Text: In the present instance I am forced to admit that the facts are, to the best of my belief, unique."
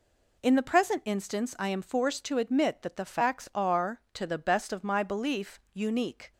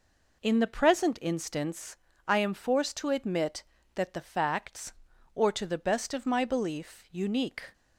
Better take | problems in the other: first | pauses between "instance" and "I"; slight; at 1.9 s; 0.28 s long // says "or" for "are"; at 5.3 s

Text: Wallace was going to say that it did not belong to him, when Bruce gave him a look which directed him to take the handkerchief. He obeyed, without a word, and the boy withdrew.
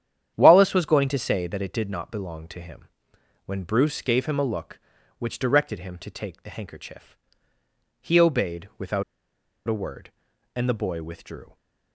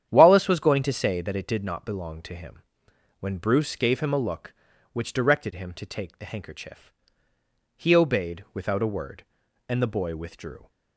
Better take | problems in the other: second | starts louder than the rest; strong; until 1.3 s; 9.5 dB; strong in the second // pauses between "without" and "a"; noticeable; at 9.0 s; 0.64 s long

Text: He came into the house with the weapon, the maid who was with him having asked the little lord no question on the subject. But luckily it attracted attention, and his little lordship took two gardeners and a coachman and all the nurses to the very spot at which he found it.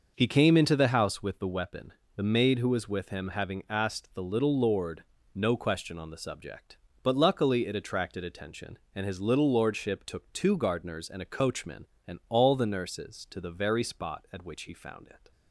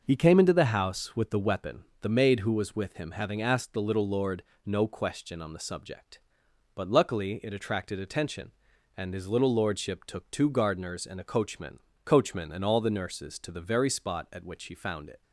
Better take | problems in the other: first | starts louder than the rest; noticeable; until 1.0 s; 6 dB; noticeable in the first // pauses between "lord" and "no"; slight; at 4.4 s; 0.24 s long; slight in the first // says "coachman" twice; at 12.0 s

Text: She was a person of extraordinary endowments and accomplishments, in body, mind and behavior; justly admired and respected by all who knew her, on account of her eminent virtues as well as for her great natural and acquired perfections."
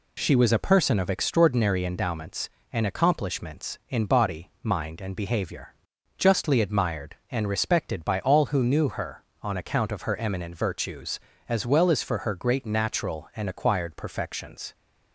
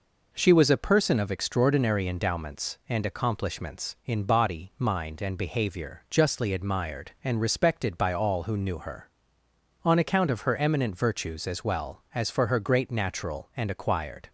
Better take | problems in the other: first | stops before "perfections"; at 14.2 s

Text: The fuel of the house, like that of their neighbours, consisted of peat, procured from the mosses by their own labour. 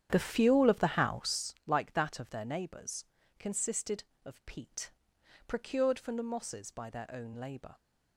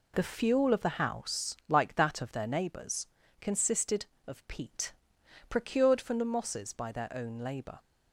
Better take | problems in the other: second | starts louder than the rest; strong; until 1.5 s; 9.5 dB

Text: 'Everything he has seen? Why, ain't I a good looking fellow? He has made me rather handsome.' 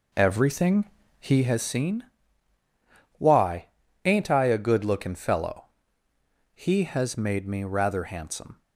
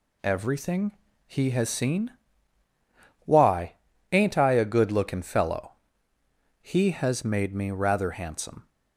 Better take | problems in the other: second | starts louder than the rest; noticeable; until 1.6 s; 4.5 dB // pauses between "Everything" and "he"; slight; at 0.8 s; 0.36 s long; slight in the second

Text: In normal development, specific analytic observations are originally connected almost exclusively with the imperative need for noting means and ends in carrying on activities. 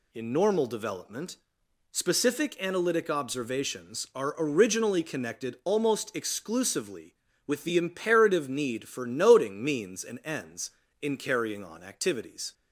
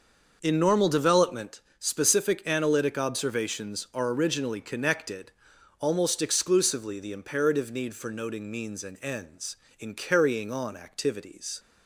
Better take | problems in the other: first | starts louder than the rest; until 1.4 s; 6 dB // pauses between "connected" and "almost"; noticeable; at 5.3 s; 0.50 s long // skips "with"; at 6.9 s

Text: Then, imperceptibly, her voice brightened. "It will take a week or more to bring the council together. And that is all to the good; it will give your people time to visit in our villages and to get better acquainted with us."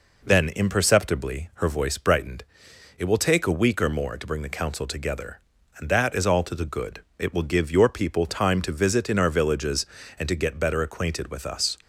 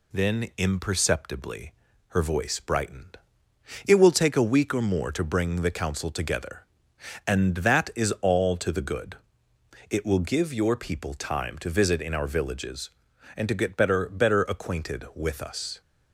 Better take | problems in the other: first | says "better" twice; at 14.0 s

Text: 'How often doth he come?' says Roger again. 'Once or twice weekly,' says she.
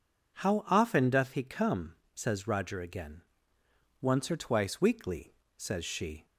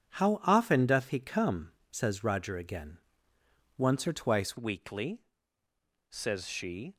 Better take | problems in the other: first | changes voice at "weekly"; from 4.5 s on; 2.4 s long

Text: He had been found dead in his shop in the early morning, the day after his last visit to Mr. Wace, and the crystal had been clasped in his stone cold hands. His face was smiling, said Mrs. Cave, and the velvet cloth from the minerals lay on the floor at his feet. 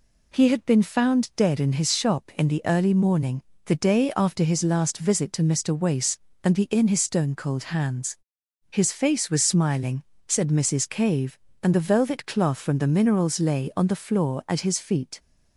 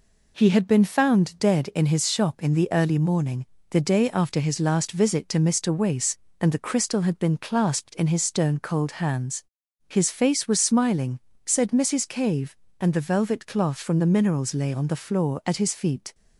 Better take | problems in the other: second | skips "crystal had been clasped"; at 6.6 s

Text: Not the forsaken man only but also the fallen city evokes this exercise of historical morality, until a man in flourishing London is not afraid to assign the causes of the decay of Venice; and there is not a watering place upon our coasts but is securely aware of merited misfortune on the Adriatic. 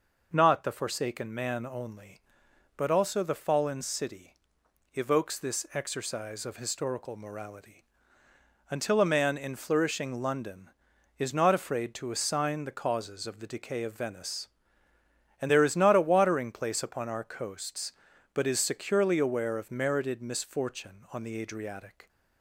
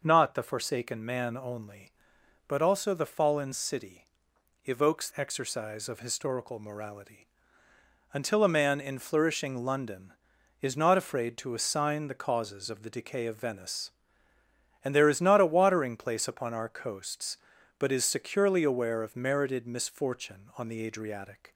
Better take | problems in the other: first | pauses between "city" and "evokes"; noticeable; at 4.0 s; 0.56 s long; noticeable in the first // skips "this"; at 5.1 s

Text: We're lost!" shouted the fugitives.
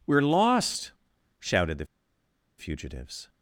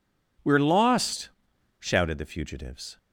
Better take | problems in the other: second | pauses between "the" and "fugitives"; noticeable; at 1.8 s; 0.72 s long

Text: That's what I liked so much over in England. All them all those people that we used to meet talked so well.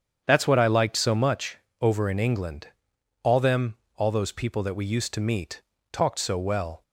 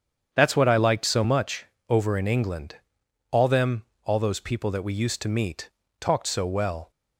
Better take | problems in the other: neither | starts louder than the rest; strong; the same in both // pauses between "much" and "over"; slight; the same in both // pauses between "them" and "all"; slight; the same in both // pauses between "meet" and "talked"; slight; the same in both

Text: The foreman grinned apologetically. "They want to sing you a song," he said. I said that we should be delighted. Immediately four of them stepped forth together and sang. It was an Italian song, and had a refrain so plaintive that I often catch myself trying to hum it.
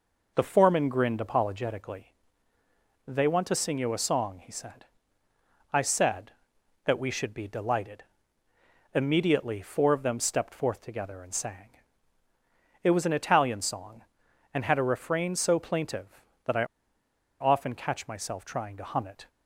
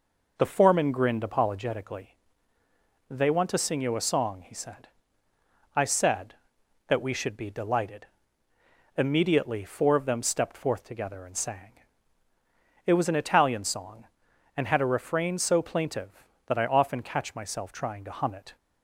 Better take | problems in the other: second | pauses between "I" and "often"; noticeable; at 16.6 s; 0.74 s long

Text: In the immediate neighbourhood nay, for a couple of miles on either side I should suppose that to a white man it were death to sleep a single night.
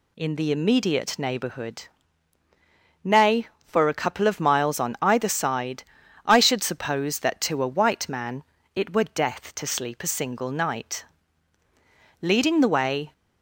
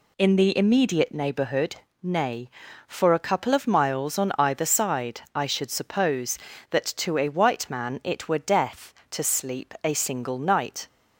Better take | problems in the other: second | pauses between "neighbourhood" and "nay"; at 1.8 s; 1.1 s long; slight in the second // pauses between "side" and "I"; at 5.8 s; 0.42 s long // pauses between "man" and "it"; slight; at 8.4 s; 0.32 s long // goes on to say "Leading the way"; noticeable; from 12.2 s on; 0.92 s long

